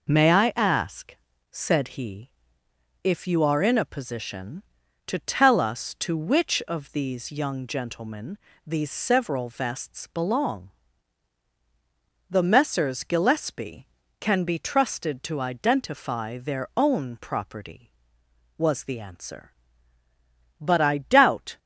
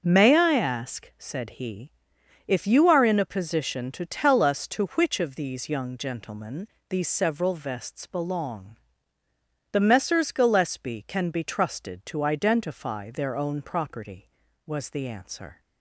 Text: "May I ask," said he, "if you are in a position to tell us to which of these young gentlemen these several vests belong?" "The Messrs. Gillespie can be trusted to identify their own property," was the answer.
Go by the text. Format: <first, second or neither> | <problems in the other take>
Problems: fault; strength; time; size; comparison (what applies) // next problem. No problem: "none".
second | pauses between "gentlemen" and "these"; slight; at 8.3 s; 0.28 s long; slight in the second // goes on to say "But I doubt"; noticeable; from 20.5 s on; 1.0 s long